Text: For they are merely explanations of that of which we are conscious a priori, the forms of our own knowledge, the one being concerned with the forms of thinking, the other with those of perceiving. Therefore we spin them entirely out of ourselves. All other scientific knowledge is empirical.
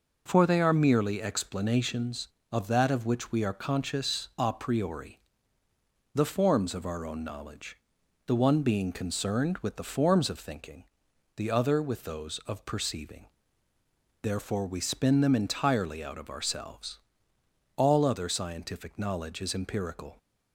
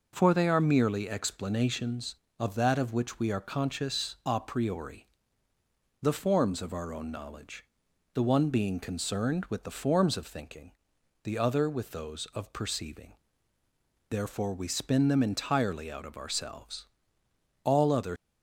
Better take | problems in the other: first | stops before "scientific knowledge is empirical"; at 18.1 s

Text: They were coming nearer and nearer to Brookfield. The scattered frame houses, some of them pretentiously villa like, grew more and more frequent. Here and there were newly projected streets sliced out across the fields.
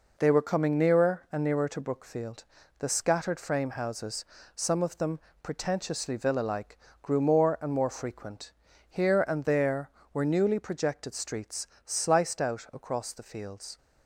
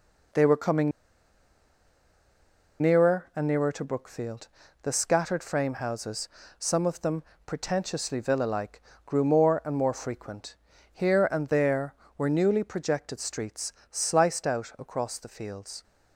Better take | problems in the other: first | pauses between "coming" and "nearer"; strong; at 0.9 s; 1.9 s long // pauses between "them" and "pretentiously"; slight; at 7.2 s; 0.24 s long; slight in the first // pauses between "streets" and "sliced"; slight; at 13.7 s; 0.18 s long; slight in the first

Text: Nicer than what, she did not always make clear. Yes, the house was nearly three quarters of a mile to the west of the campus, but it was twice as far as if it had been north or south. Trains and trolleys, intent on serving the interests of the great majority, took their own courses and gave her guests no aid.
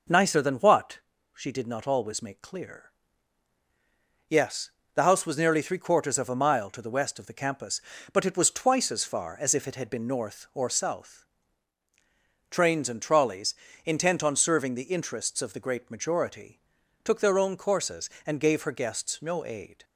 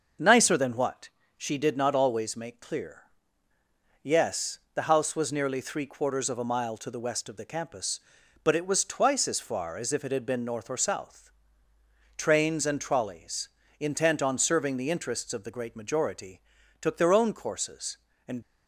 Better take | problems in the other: first | starts louder than the rest; until 1.5 s; 6 dB // stops before "gave her guests no aid"; at 18.4 s

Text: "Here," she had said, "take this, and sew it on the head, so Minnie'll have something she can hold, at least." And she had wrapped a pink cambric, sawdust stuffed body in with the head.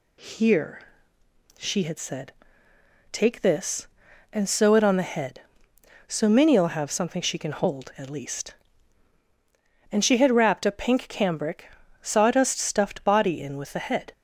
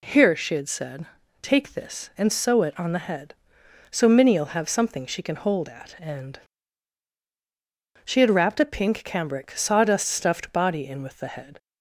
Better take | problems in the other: first | skips "least"; at 5.9 s // pauses between "And" and "she"; strong; at 6.3 s; 1.6 s long

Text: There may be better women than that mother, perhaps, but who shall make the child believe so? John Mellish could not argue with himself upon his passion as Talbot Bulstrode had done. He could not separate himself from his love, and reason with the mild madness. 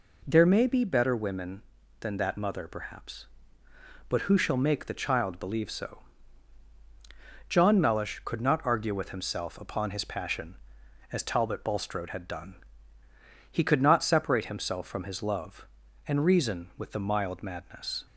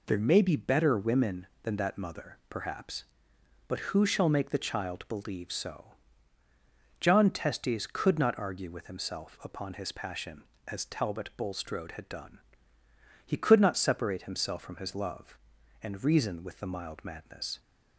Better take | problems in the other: first | says "Testes" for "Mellish"; at 7.3 s

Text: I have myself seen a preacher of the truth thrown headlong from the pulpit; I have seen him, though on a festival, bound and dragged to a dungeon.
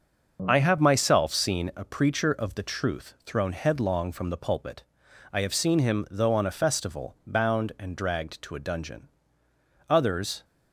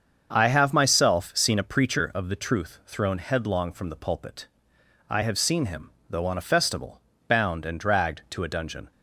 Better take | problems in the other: second | starts louder than the rest; until 1.4 s; 6.5 dB; also in the second // goes on to say "Others"; from 9.9 s on; 0.54 s long

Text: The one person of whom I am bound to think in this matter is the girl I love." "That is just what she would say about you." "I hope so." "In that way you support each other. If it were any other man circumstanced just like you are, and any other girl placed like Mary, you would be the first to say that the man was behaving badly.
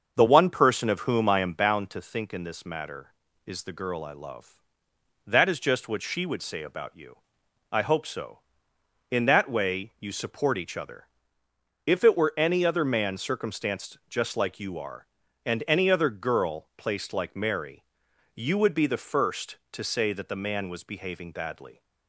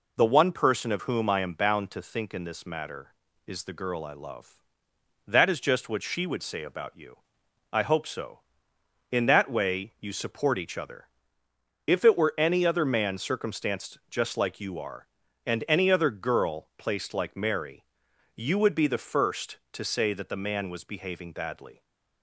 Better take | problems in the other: second | starts louder than the rest; until 1.8 s; 6.5 dB

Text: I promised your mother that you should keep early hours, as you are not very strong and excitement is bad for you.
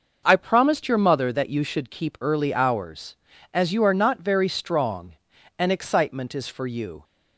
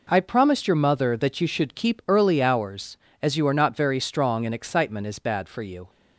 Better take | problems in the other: second | skips "bad"; at 6.4 s

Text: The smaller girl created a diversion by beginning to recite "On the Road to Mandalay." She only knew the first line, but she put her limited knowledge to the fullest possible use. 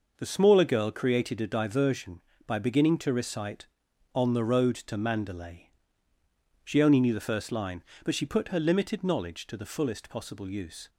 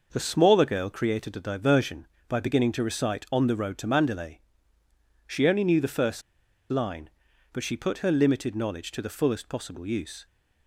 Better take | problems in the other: first | pauses between "first" and "line"; noticeable; at 6.2 s; 0.48 s long

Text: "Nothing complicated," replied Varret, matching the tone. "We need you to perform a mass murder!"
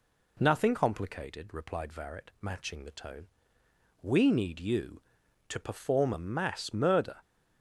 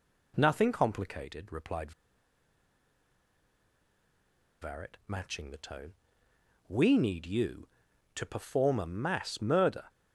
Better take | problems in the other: first | pauses between "replied" and "Varret"; strong; at 1.9 s; 2.6 s long

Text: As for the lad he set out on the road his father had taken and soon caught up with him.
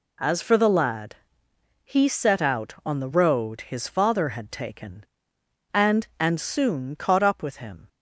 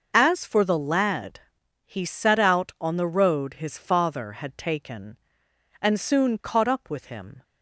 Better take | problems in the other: second | pauses between "lad" and "he"; noticeable; at 1.1 s; 0.70 s long; also in the second // says "and" twice; at 6.1 s

